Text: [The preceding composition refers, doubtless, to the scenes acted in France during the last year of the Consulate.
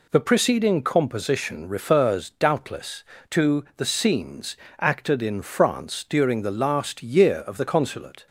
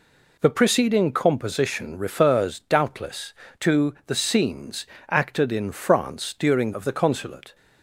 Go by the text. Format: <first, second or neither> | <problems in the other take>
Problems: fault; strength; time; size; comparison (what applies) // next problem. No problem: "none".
first | pauses between "scenes" and "acted"; slight; at 4.8 s; 0.24 s long; slight in the first // skips "the last year"; at 6.7 s